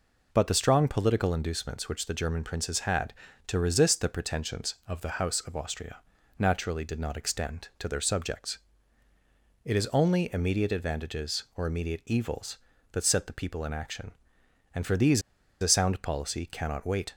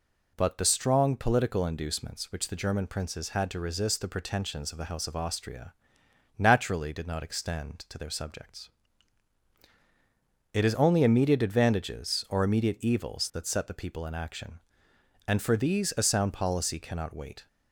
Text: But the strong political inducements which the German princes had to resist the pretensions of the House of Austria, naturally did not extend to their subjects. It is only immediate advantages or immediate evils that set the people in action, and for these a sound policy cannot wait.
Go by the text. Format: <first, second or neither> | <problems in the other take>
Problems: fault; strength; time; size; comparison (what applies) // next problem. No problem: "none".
second | pauses between "these" and "a"; at 15.2 s; 0.39 s long